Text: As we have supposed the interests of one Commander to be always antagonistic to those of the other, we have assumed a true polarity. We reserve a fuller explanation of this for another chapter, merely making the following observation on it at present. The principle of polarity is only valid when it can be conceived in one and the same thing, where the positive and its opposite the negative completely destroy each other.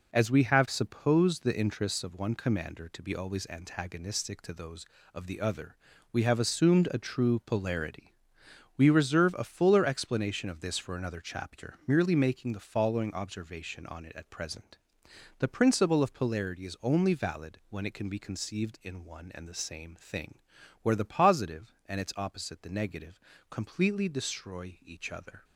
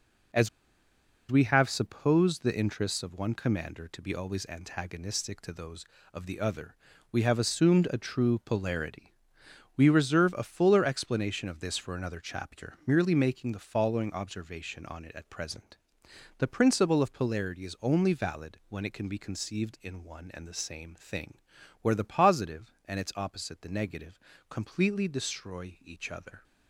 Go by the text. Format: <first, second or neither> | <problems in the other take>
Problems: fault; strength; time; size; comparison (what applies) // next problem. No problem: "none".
first | pauses between "As" and "we"; noticeable; at 0.4 s; 0.82 s long // pauses between "negative" and "completely"; slight; at 24.1 s; 0.30 s long; slight in the first